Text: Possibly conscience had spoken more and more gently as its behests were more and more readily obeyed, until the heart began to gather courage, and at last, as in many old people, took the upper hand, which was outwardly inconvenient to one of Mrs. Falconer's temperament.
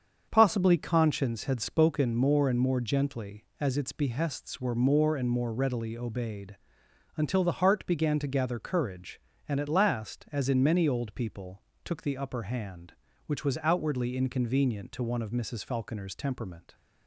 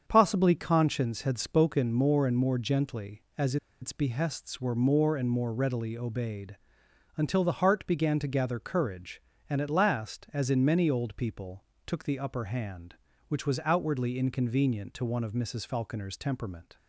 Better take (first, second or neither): first